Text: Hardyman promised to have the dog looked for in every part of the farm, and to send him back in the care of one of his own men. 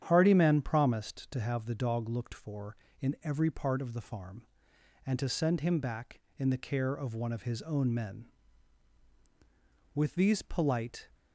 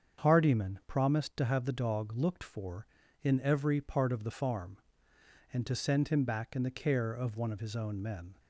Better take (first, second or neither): second